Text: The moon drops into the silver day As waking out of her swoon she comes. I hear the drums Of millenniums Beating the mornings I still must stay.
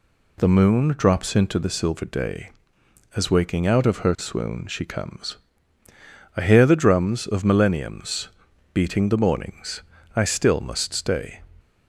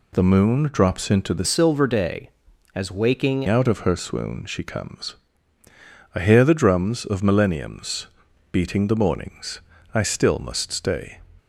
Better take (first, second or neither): first